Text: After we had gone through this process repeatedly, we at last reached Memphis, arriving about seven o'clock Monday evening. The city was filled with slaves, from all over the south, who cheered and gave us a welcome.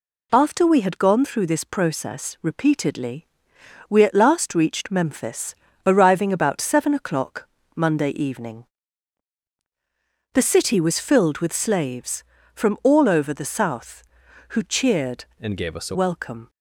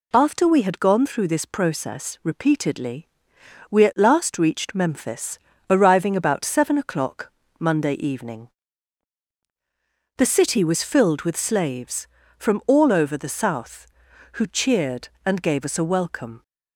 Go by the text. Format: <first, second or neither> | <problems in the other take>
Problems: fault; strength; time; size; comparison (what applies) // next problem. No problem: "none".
second | pauses between "o'clock" and "Monday"; slight; at 7.4 s; 0.30 s long; slight in the second // changes voice from "and" to "a"; from 15.4 to 15.9 s; 0.5 s long